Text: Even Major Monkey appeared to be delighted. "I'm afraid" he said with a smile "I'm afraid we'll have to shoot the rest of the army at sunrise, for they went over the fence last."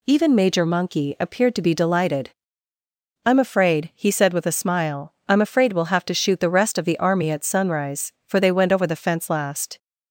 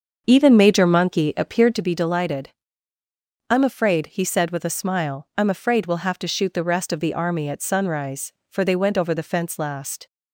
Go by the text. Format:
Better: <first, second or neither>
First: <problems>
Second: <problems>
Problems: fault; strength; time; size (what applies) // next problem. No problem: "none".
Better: first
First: none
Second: starts louder than the rest; until 1.9 s; 6.5 dB